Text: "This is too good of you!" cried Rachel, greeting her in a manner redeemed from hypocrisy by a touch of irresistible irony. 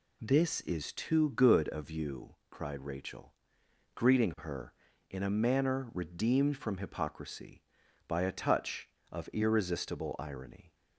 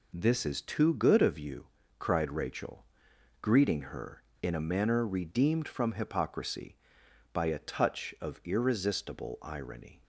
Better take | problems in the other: neither | none

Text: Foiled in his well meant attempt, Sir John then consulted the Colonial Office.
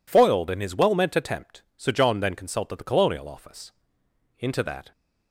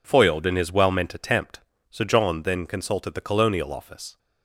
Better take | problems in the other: second | goes on to say "Into that"; from 4.3 s on; 0.52 s long

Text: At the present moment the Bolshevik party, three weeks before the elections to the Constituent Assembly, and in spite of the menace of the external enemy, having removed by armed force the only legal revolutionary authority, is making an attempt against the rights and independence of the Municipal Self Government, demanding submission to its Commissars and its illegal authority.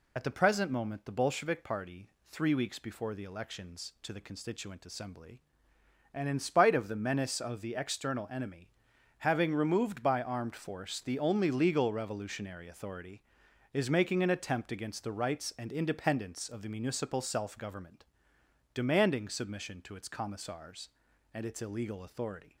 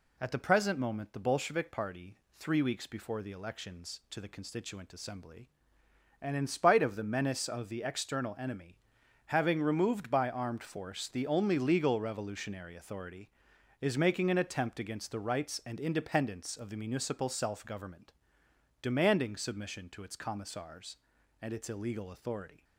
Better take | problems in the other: second | loses the start of "At"; at 0.1 s; 40 ms

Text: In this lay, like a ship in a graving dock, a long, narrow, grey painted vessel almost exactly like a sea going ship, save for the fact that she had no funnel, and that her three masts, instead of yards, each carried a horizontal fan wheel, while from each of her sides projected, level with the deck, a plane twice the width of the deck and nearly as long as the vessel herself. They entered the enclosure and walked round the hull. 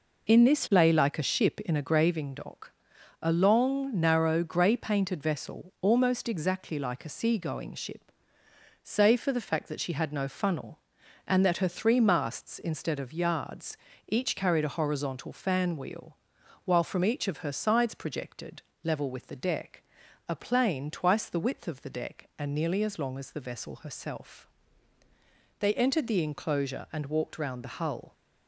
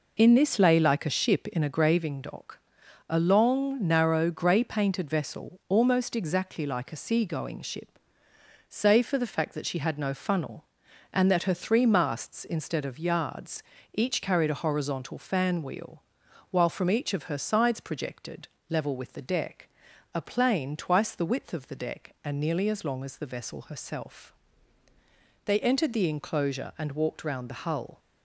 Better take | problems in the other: neither | none

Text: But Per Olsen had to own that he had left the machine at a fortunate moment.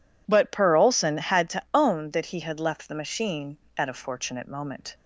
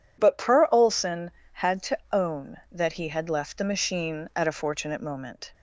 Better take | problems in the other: neither | none

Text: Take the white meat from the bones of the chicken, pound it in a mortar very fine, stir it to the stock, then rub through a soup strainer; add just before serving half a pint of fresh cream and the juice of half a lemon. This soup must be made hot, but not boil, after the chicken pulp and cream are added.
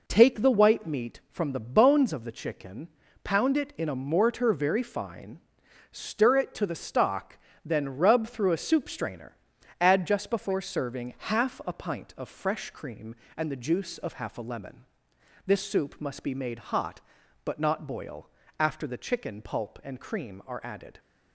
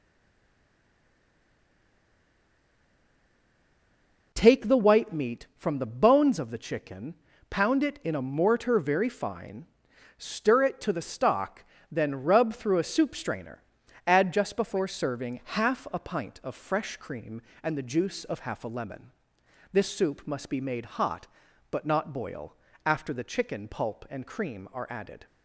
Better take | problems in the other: first | stays silent before the first word; strong; until 4.3 s; 4.3 s long

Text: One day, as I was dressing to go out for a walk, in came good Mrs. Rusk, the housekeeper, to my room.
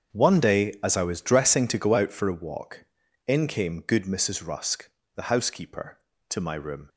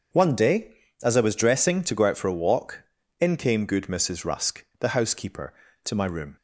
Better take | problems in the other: second | gets quieter; strong; throughout; 14 dB // starts louder than the rest; strong; until 1.2 s; 7.5 dB; also in the second

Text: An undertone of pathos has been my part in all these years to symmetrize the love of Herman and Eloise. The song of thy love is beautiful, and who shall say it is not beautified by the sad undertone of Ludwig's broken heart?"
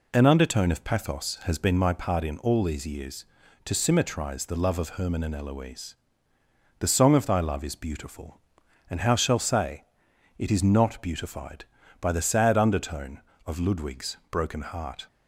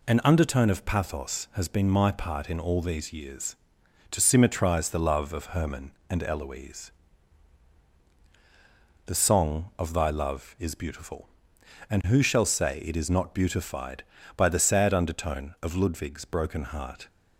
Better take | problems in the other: second | says "how" for "who"; at 9.0 s // pauses between "say" and "it"; noticeable; at 9.8 s; 0.56 s long

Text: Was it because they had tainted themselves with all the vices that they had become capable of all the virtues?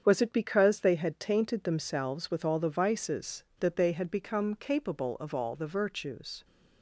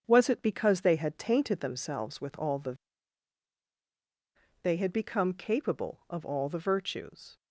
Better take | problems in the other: first | starts louder than the rest; strong; until 1.0 s; 7 dB; strong in the first // skips "vices that"; at 3.6 s

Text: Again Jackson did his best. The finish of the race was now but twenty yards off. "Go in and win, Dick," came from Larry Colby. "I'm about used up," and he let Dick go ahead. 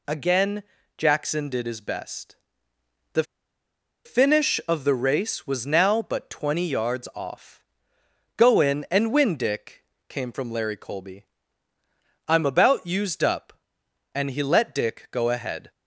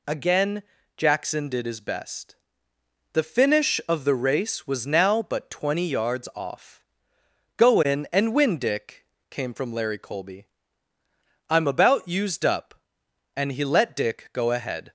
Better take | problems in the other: second | pauses between "Again" and "Jackson"; slight; at 0.6 s; 0.34 s long; slight in the second // pauses between "The" and "finish"; noticeable; at 3.2 s; 0.82 s long

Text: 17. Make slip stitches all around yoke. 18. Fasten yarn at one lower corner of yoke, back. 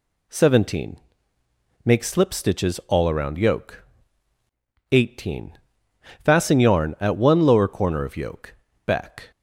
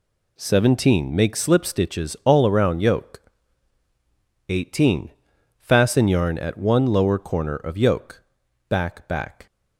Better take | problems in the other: first | says "back" twice; at 9.0 s

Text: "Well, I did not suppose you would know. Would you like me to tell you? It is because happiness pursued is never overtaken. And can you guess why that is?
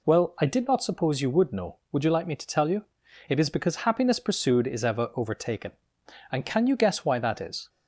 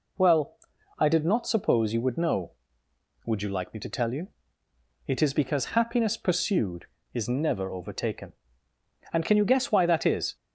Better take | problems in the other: second | says "ever" for "never"; at 4.8 s

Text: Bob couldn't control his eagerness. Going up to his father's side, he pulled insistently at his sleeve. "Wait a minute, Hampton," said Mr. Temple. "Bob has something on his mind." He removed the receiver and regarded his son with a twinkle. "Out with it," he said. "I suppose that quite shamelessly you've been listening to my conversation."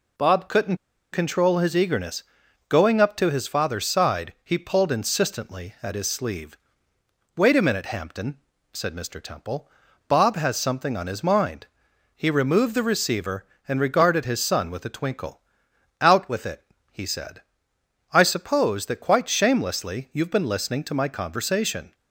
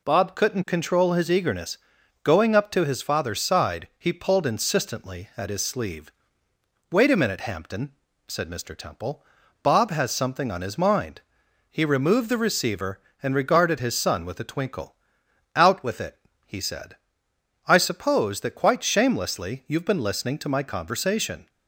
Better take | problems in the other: second | pauses between "couldn't" and "control"; slight; at 0.7 s; 0.35 s long

